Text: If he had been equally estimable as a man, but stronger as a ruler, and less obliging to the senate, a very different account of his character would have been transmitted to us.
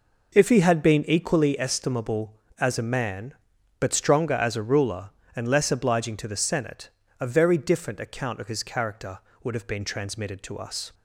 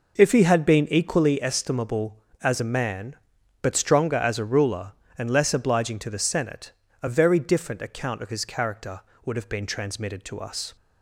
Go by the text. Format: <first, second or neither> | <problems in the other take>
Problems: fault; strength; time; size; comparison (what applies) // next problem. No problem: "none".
neither | none